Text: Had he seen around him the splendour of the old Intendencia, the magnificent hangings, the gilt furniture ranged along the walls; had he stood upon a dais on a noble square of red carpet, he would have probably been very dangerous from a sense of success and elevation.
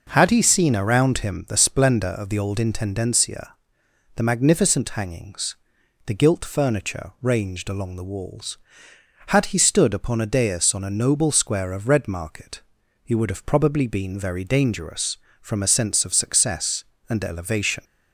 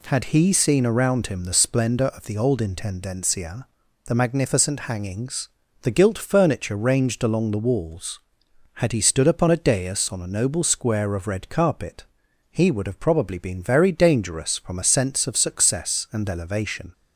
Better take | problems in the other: second | says "market" for "carpet"; at 12.0 s

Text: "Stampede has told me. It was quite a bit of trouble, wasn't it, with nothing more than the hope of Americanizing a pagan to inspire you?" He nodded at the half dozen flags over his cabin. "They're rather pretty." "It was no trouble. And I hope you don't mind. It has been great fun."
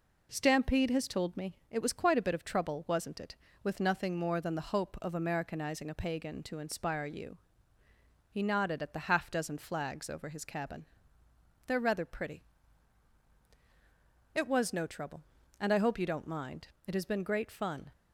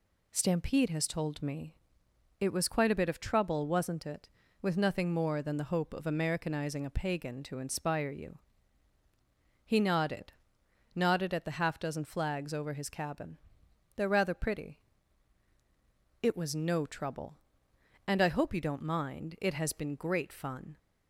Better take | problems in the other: first | says "nodded" twice; at 10.9 s

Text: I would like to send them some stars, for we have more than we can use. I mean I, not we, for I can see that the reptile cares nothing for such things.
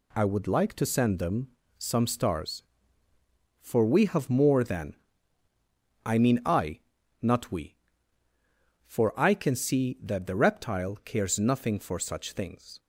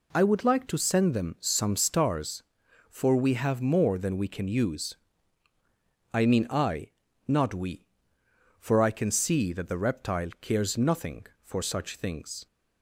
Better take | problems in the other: second | pauses between "them" and "some"; slight; at 1.4 s; 0.30 s long // skips "we can use"; at 5.5 s

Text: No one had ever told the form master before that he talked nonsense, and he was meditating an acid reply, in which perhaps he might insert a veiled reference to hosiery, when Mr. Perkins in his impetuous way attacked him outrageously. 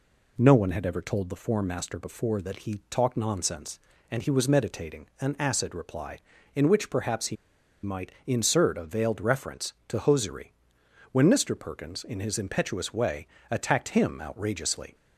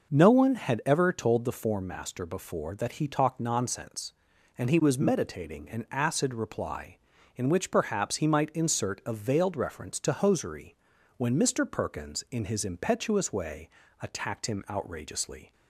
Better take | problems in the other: second | pauses between "he" and "might"; noticeable; at 7.3 s; 0.48 s long // pauses between "way" and "attacked"; slight; at 13.2 s; 0.24 s long; slight in the second

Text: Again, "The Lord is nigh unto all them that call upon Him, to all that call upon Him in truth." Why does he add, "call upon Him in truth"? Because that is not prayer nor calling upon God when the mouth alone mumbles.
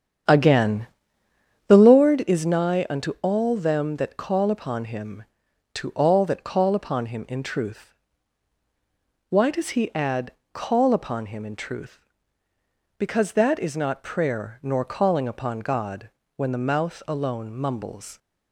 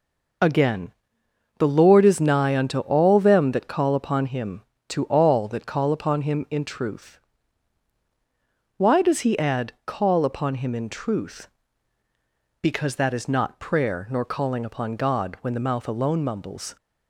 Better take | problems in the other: second | starts louder than the rest; strong; until 2.1 s; 8.5 dB // pauses between "God" and "when"; slight; at 16.0 s; 0.28 s long

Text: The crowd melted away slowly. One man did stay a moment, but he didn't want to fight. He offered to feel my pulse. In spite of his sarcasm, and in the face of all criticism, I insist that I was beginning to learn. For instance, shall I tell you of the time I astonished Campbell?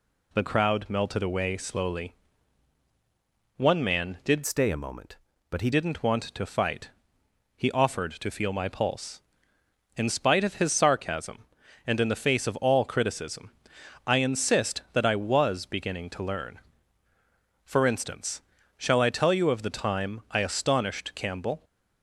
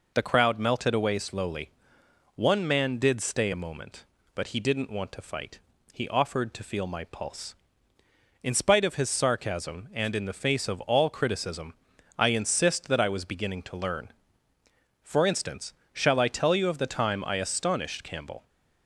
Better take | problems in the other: second | changes voice from "stay" to "he"; from 4.4 to 5.7 s; 1.3 s long

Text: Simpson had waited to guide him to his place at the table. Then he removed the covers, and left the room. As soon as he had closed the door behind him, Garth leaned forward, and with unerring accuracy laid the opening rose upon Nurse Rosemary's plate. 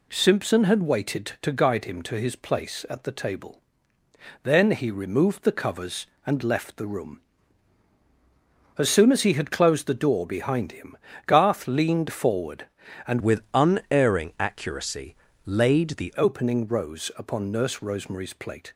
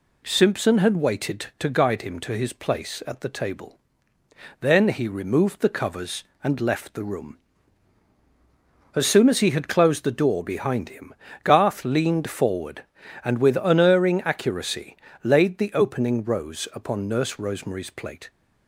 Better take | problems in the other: second | changes voice from "with" to "the"; from 13.2 to 16.1 s; 2.9 s long // pauses between "accuracy" and "laid"; slight; at 15.1 s; 0.30 s long; slight in the second

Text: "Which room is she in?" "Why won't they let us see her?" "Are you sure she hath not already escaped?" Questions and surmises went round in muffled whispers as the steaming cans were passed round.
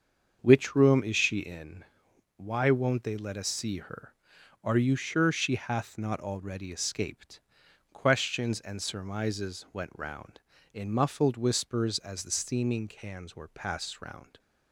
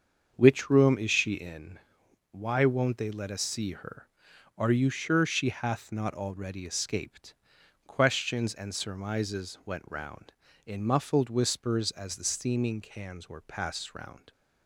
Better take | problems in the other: neither | starts louder than the rest; the same in both

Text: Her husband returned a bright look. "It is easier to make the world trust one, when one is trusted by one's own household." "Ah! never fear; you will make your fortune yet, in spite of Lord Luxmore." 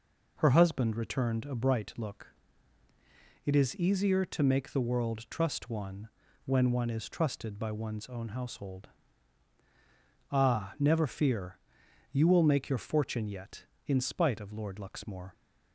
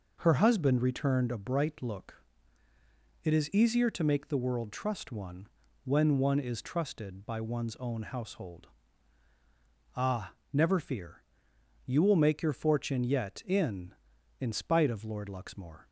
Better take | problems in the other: first | says "in" twice; at 14.4 s

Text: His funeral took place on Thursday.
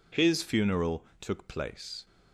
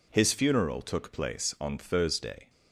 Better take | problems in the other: second | pauses between "funeral" and "took"; slight; at 1.0 s; 0.18 s long // stops before "on Thursday"; at 2.0 s

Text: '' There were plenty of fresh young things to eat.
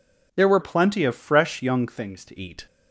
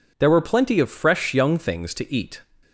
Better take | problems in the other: second | changes voice from "plenty" to "to"; from 0.6 to 2.3 s; 1.7 s long

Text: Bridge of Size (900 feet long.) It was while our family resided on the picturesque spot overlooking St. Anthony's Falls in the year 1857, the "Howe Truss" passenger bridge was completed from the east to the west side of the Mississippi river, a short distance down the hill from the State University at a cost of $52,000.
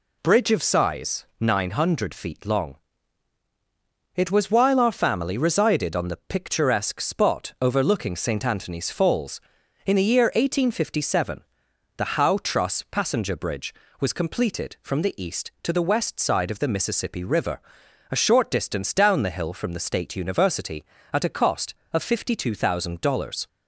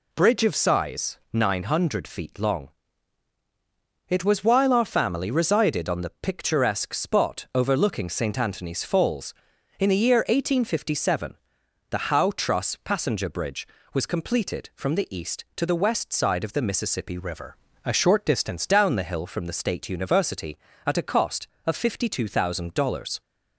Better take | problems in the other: first | changes voice from "river" to "distance"; from 17.1 to 18.6 s; 1.5 s long

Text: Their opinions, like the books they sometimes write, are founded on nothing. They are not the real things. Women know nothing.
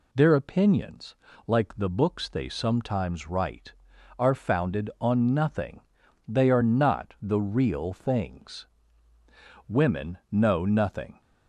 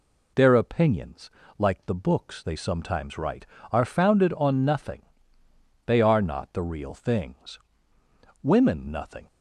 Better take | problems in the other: first | skips "know"; at 8.8 s

